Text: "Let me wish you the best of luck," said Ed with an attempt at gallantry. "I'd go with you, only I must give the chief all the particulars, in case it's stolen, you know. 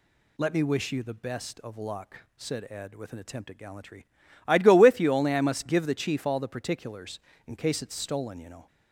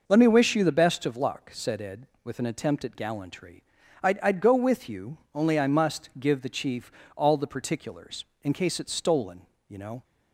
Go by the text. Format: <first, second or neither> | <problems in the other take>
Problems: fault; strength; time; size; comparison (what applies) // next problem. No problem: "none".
first | says "I'd" twice; at 4.2 s // pauses between "chief" and "all"; slight; at 6.9 s; 0.24 s long